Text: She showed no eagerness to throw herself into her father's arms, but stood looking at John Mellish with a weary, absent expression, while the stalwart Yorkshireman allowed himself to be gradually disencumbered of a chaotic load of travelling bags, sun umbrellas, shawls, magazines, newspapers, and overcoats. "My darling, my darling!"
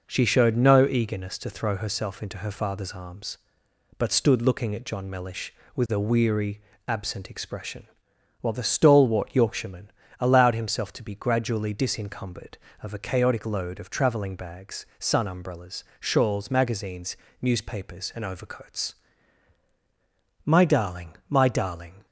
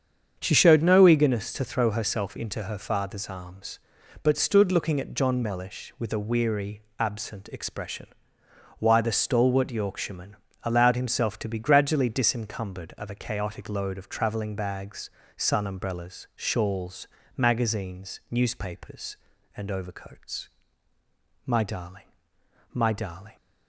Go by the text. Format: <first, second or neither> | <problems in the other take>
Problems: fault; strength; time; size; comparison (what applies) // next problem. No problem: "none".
first | starts louder than the rest; strong; until 1.4 s; 7.5 dB // says "why" for "while"; at 8.7 s // pauses between "Yorkshireman" and "allowed"; slight; at 10.3 s; 0.28 s long; slight in the first